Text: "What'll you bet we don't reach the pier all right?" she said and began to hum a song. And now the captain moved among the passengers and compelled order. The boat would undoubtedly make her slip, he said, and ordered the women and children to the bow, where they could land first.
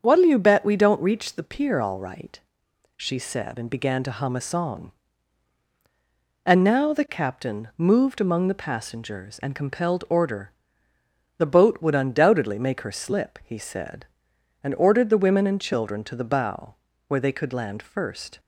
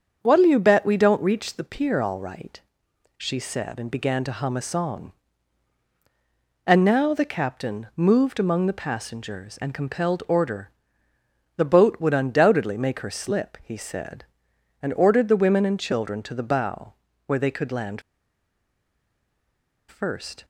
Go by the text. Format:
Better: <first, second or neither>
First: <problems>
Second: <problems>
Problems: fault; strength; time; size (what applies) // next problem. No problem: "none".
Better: first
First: starts louder than the rest; strong; until 1.0 s; 7 dB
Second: starts louder than the rest; strong; until 1.2 s; 7 dB // pauses between "land" and "first"; strong; at 18.0 s; 1.8 s long